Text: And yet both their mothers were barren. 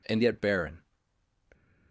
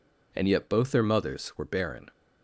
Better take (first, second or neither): second